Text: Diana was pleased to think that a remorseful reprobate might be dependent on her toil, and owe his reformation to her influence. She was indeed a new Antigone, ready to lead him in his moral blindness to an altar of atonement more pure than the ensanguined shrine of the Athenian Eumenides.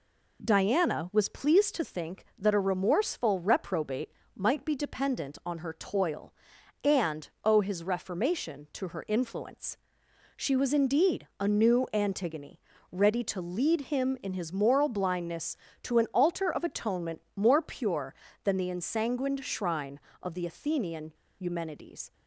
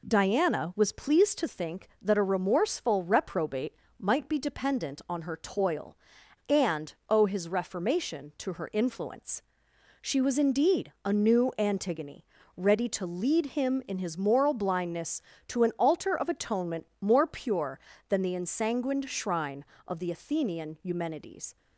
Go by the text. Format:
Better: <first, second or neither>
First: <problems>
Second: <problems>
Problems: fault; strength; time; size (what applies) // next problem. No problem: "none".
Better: second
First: pauses between "reprobate" and "might"; slight; at 4.0 s; 0.26 s long // pauses between "and" and "owe"; slight; at 7.2 s; 0.16 s long // pauses between "Athenian" and "Eumenides"; slight; at 21.1 s; 0.27 s long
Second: pauses between "reprobate" and "might"; slight; at 3.7 s; 0.26 s long // pauses between "and" and "owe"; slight; at 6.9 s; 0.16 s long